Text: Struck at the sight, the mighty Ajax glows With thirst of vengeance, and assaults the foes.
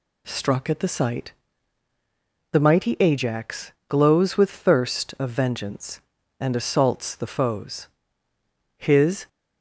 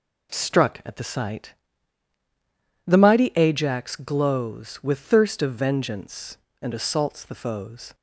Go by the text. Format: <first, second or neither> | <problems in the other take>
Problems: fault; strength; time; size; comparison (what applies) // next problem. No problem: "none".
second | pauses between "Ajax" and "glows"; slight; at 3.6 s; 0.18 s long // goes on to say "His"; from 8.7 s on; 0.52 s long